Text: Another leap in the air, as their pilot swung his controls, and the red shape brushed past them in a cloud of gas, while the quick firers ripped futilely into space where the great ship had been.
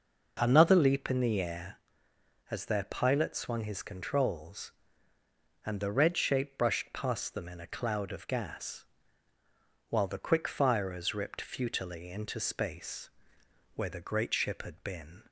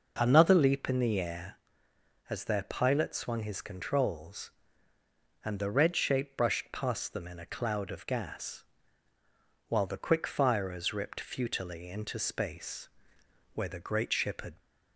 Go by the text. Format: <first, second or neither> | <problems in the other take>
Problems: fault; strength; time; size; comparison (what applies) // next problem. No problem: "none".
first | pauses between "space" and "where"; noticeable; at 12.8 s; 0.64 s long; noticeable in the first // stops before "been"; at 14.6 s